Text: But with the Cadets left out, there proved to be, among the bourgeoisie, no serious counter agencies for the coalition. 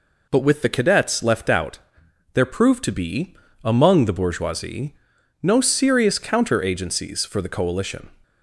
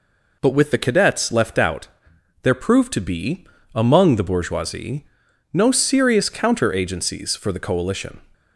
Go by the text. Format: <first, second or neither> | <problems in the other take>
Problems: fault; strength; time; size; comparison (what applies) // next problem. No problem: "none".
neither | none